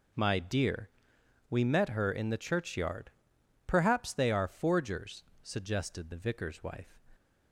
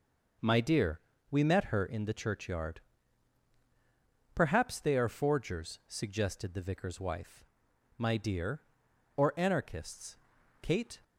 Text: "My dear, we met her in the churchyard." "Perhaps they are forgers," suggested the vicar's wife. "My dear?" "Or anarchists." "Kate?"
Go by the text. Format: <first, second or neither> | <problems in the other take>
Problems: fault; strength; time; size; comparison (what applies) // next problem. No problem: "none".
second | stops before "My dear Or anarchists Kate"; at 7.1 s